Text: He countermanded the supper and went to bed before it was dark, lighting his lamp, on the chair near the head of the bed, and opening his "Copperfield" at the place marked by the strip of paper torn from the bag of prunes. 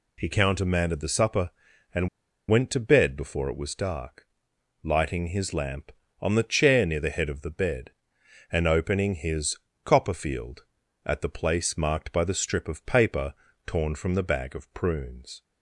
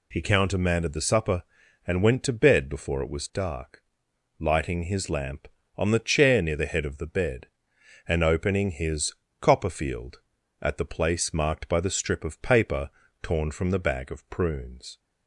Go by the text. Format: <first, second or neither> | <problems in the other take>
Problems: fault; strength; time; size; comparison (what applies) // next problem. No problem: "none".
second | pauses between "and" and "went"; at 2.0 s; 0.42 s long // pauses between "his" and "Copperfield"; slight; at 9.5 s; 0.28 s long; slight in the second // pauses between "paper" and "torn"; slight; at 13.3 s; 0.34 s long; slight in the second